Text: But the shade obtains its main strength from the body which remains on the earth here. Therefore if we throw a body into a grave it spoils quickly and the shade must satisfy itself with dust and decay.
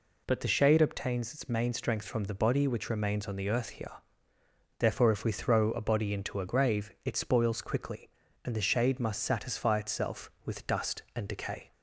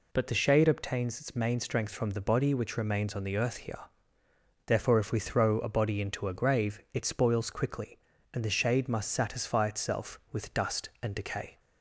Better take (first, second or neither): neither